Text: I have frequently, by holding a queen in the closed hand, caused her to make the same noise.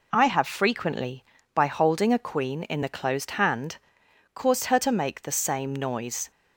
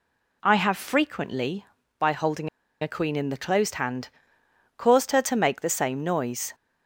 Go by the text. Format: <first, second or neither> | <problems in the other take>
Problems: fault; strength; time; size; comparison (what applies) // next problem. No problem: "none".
first | pauses between "holding" and "a"; slight; at 2.4 s; 0.33 s long